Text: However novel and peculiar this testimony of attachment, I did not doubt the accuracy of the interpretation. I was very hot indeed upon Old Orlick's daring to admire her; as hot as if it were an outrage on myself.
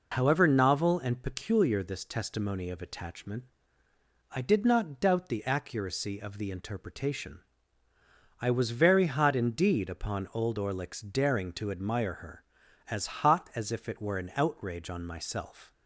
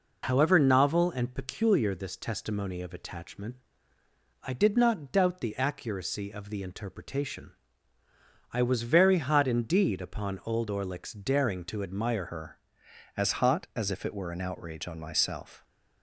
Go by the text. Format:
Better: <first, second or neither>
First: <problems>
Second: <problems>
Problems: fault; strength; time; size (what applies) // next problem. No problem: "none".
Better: first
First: none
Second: changes voice at "her"; from 12.2 s on; 3.4 s long